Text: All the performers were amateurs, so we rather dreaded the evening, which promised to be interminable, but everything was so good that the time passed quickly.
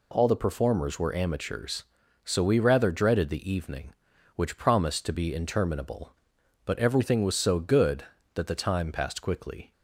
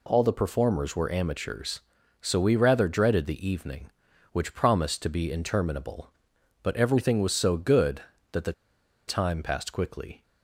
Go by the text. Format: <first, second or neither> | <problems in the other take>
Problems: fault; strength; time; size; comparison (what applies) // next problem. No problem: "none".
first | pauses between "the" and "time"; noticeable; at 8.5 s; 0.54 s long